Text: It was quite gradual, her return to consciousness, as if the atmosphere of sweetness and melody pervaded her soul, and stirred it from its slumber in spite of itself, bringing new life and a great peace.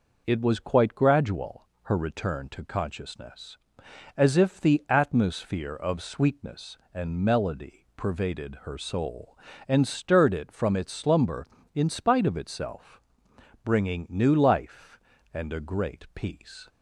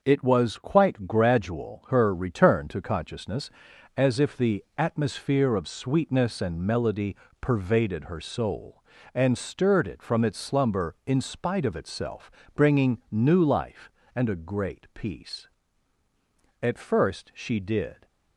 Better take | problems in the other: first | starts louder than the rest; until 1.0 s; 6.5 dB // pauses between "melody" and "pervaded"; slight; at 7.1 s; 0.24 s long // goes on to say "At first she did"; from 16.6 s on; 1.4 s long

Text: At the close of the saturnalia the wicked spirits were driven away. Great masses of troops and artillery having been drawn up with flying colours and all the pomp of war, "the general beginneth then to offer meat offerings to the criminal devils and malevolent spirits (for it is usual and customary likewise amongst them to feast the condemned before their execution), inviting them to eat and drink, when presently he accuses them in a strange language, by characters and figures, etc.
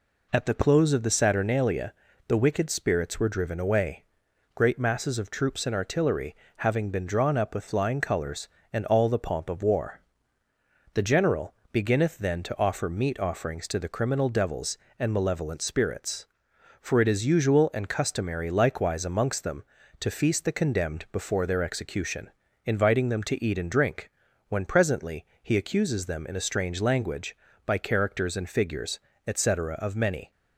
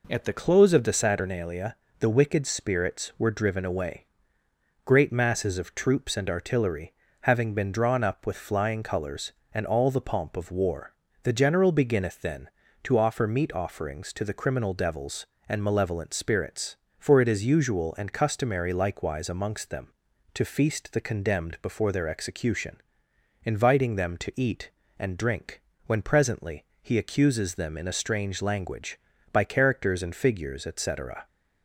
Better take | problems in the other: second | pauses between "saturnalia" and "the"; slight; at 1.9 s; 0.32 s long; slight in the second // pauses between "artillery" and "having"; slight; at 6.3 s; 0.22 s long; slight in the second // pauses between "general" and "beginneth"; slight; at 11.5 s; 0.18 s long // pauses between "presently" and "he"; slight; at 25.2 s; 0.16 s long; slight in the second // goes on to say "of many"; from 29.7 s on; 0.56 s long

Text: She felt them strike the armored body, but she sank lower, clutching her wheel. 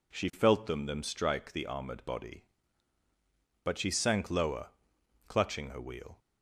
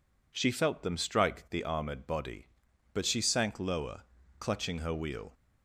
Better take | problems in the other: second | says "them" twice; at 0.8 s

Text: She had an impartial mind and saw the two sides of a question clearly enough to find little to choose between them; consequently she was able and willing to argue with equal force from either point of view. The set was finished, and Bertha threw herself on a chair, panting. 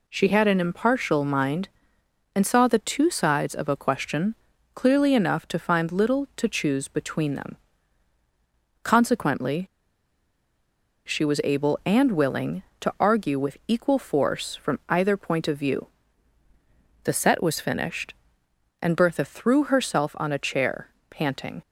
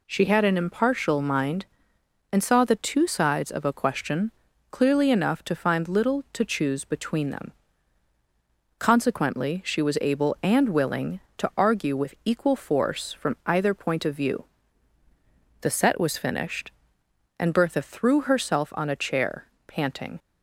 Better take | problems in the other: second | pauses between "question" and "clearly"; at 4.3 s; 0.40 s long; also in the second // pauses between "consequently" and "she"; strong; at 9.6 s; 1.4 s long

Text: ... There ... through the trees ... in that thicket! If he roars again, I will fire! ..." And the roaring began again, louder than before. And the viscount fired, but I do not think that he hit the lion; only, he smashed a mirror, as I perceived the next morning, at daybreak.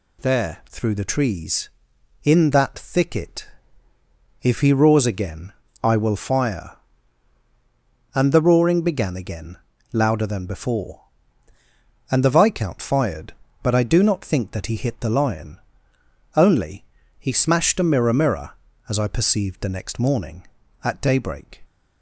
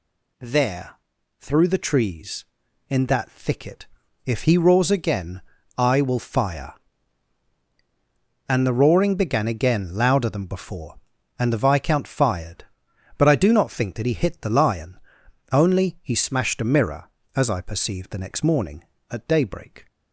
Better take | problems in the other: second | says "mirror" twice; at 18.1 s

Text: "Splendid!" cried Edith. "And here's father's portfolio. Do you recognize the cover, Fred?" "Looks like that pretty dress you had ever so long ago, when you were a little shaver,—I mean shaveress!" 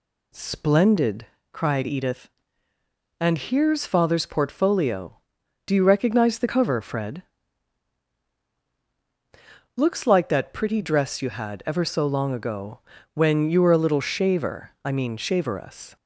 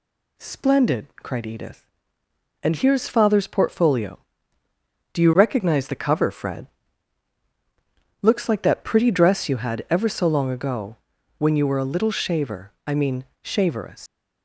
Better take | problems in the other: first | pauses between "mean" and "shaveress"; slight; at 13.2 s; 0.18 s long // leaves "shaveress" unfinished; at 14.0 s; 140 ms

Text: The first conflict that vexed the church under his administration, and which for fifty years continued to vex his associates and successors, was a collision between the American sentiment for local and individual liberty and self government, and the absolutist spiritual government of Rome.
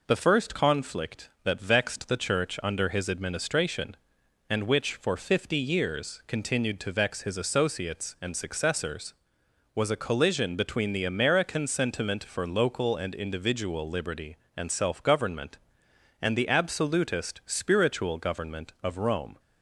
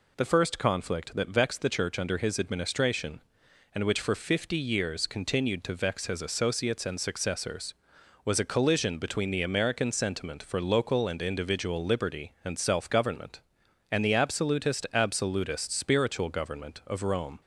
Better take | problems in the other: first | says "absolutist" twice; at 14.9 s

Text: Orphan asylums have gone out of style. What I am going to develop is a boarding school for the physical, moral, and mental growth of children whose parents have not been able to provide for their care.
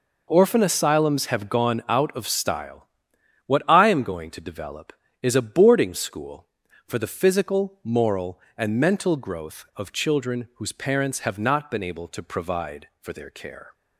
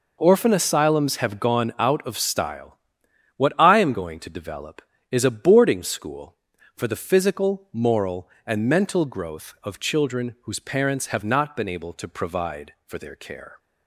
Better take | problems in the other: neither | none

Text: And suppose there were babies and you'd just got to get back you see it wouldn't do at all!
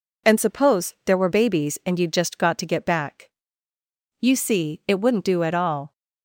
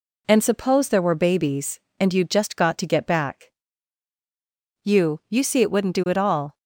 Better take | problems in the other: first | pauses between "back" and "you"; strong; at 3.5 s; 1.3 s long; noticeable in the first // says "you" twice; at 5.2 s

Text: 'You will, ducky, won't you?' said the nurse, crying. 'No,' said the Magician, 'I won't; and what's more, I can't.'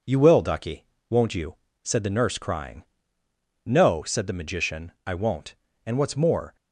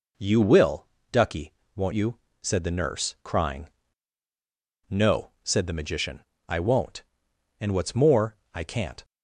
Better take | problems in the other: second | stops before "I can't"; at 6.5 s

